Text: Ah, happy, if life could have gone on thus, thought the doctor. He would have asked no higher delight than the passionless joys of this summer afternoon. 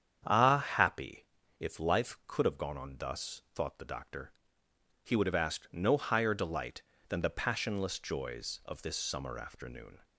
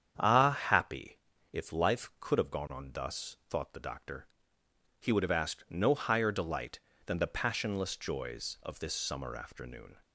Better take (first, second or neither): neither